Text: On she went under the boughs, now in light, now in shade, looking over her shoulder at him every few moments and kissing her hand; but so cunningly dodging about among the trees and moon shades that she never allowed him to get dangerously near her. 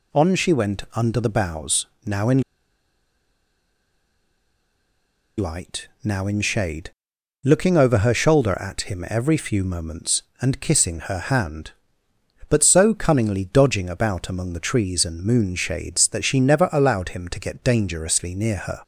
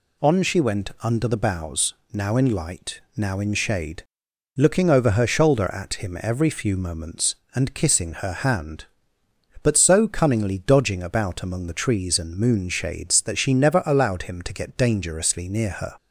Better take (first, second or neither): second